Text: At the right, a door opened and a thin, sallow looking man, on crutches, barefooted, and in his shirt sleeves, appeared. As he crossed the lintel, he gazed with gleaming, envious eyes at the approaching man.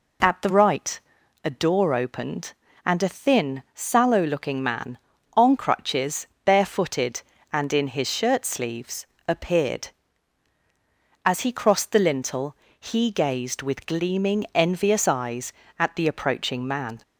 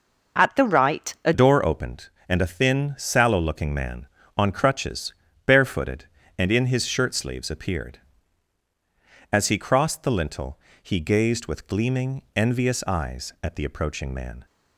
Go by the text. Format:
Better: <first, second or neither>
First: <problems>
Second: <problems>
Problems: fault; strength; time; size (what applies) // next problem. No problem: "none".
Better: first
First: none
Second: changes voice at "door"; from 1.3 s on; 13.1 s long